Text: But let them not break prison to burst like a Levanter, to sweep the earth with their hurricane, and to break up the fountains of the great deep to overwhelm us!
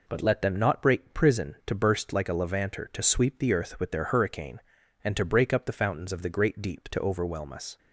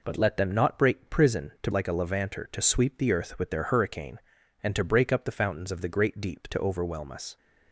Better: first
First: none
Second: skips "burst"; at 1.7 s

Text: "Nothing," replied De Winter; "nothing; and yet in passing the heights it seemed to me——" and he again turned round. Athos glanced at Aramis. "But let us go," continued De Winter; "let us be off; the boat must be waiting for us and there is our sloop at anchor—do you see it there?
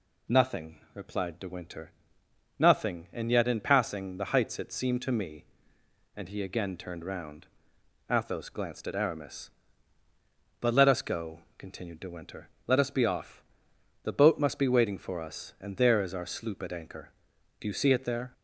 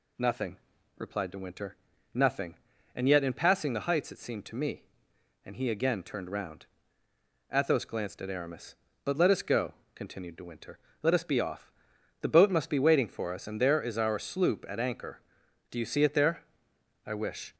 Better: first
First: none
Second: goes on to say "I wish"; slight; from 17.0 s on; 0.48 s long

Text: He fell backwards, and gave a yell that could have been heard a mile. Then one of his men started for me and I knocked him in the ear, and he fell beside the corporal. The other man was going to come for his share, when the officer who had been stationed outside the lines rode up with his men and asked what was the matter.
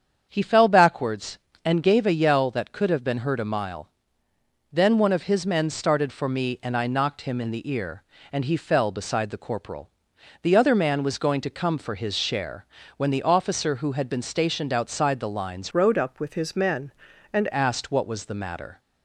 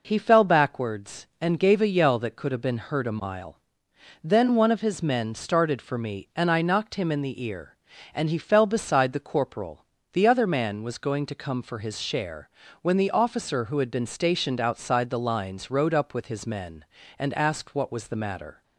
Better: second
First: starts louder than the rest; strong; until 1.3 s; 7.5 dB // changes voice from "rode" to "and"; from 15.7 to 17.4 s; 1.7 s long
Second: none

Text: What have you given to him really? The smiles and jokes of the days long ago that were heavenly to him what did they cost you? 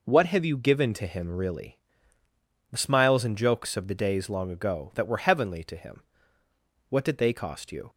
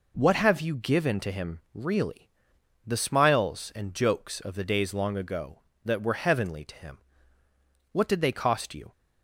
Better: neither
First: pauses between "him" and "what"; noticeable; at 6.0 s; 0.88 s long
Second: pauses between "him" and "what"; noticeable; at 6.9 s; 0.92 s long

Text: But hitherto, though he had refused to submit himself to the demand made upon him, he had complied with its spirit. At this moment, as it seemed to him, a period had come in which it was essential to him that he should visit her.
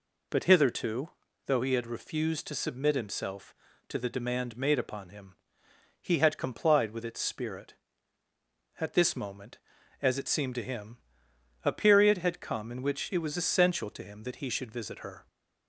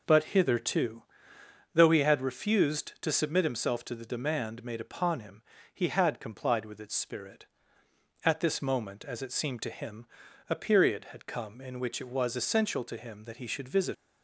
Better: first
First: none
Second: stops before "her"; at 13.9 s

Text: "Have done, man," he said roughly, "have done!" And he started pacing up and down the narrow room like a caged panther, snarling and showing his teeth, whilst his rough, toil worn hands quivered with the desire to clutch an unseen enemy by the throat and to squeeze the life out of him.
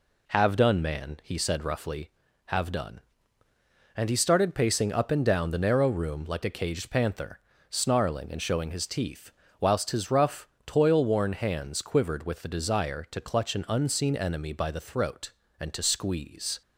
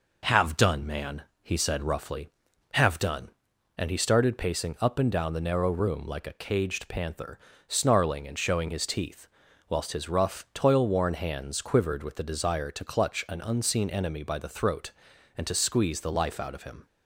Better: second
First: stops before "the life out of him"; at 16.6 s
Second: none

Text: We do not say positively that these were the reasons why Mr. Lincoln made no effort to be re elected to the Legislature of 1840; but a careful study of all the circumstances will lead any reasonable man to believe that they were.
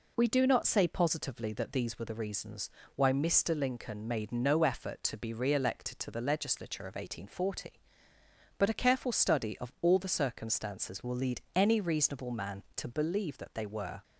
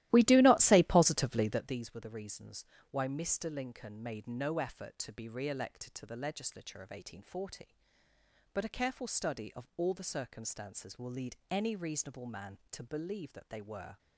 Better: first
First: pauses between "reasons" and "why"; slight; at 2.6 s; 0.26 s long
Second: starts louder than the rest; strong; until 1.8 s; 15.5 dB // pauses between "reasons" and "why"; slight; at 2.6 s; 0.26 s long

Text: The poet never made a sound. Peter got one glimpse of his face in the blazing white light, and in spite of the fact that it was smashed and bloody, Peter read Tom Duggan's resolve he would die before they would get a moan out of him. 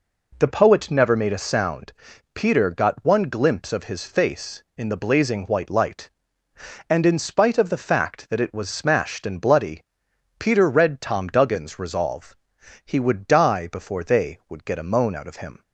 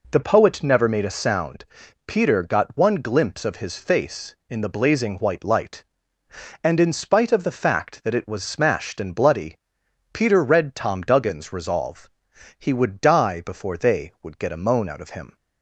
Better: neither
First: pauses between "resolve" and "he"; noticeable; at 12.3 s; 0.52 s long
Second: pauses between "resolve" and "he"; noticeable; at 12.0 s; 0.52 s long

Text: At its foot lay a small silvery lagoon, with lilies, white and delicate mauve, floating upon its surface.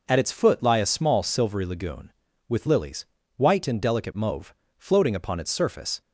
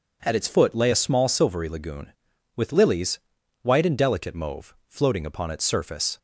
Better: second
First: says "lie" for "lay"; at 0.6 s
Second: none

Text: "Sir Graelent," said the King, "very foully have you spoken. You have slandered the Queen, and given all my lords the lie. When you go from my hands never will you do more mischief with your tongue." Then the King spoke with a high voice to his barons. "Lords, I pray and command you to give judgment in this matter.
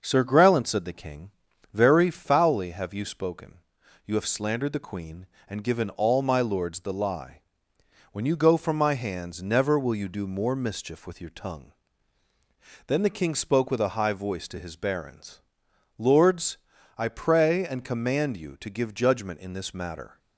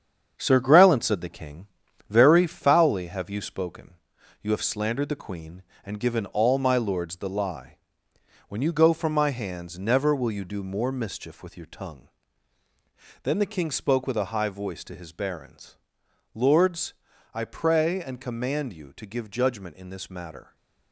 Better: first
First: none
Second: gets quieter; throughout; 7 dB

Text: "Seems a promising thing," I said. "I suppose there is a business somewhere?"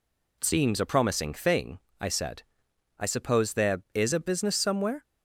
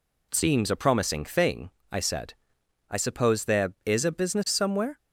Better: neither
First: none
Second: none

